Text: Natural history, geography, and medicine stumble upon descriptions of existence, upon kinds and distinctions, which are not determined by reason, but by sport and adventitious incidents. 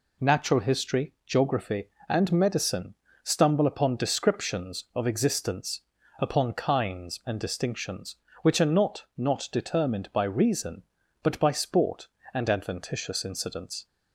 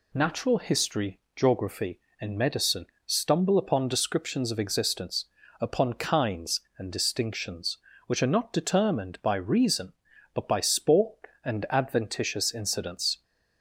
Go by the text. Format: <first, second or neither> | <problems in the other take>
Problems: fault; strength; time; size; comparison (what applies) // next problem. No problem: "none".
second | pauses between "medicine" and "stumble"; slight; at 2.9 s; 0.28 s long; slight in the second // says "not" twice; at 9.1 s